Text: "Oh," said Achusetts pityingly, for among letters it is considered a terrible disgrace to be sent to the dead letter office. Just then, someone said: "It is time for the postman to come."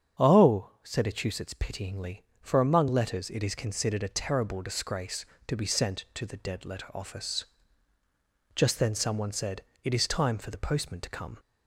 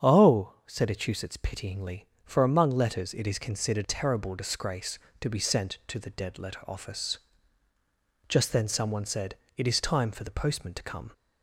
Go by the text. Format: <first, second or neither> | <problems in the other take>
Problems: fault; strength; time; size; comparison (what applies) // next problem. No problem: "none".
first | starts louder than the rest; strong; until 1.1 s; 7.5 dB; strong in the first // skips "a"; at 3.8 s